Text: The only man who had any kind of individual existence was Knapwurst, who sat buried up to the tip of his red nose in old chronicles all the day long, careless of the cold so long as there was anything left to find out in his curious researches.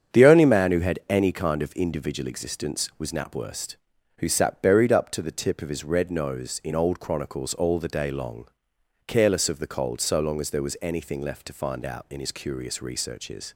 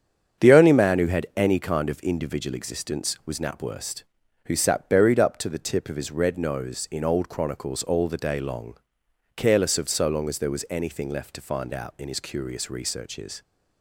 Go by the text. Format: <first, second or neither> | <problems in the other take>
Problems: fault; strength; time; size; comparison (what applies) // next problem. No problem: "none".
first | starts louder than the rest; strong; until 1.5 s; 7.5 dB; strong in the first // skips "the cold"; at 9.8 s